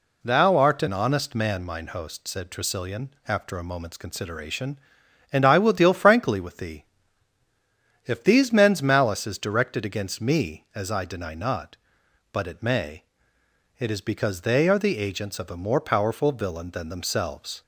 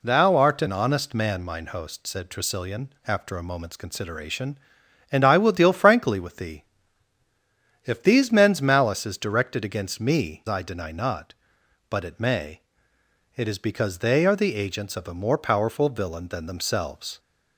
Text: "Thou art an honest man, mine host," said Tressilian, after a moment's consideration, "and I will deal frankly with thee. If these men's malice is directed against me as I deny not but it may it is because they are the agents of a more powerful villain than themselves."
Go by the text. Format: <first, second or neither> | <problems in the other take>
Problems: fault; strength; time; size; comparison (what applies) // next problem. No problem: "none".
first | skips "as"; at 10.4 s // pauses between "may" and "it"; noticeable; at 12.6 s; 0.74 s long; noticeable in the first